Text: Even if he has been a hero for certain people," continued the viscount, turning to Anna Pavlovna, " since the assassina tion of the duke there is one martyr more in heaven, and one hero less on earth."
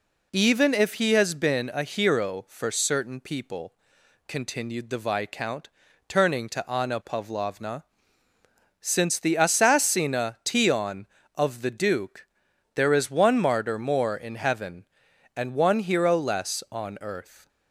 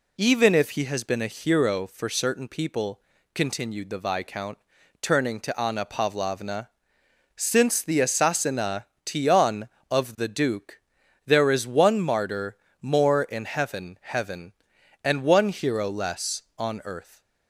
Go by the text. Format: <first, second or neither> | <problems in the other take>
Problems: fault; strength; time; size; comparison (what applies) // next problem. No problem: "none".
first | pauses between "assassina" and "tion"; slight; at 8.8 s; 0.24 s long // pauses between "duke" and "there"; noticeable; at 10.7 s; 0.48 s long; noticeable in the first // pauses between "martyr" and "more"; slight; at 12.5 s; 0.24 s long // says "heaven" twice; at 14.0 s